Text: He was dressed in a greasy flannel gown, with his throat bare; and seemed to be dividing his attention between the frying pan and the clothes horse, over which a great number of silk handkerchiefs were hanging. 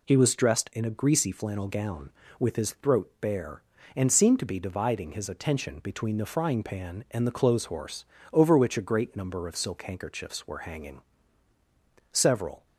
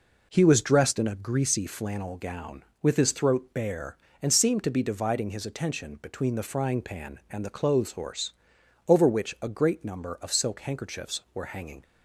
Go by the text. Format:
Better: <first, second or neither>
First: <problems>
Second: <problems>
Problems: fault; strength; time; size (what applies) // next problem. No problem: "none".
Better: second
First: goes on to say "Several"; from 12.1 s on; 0.54 s long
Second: none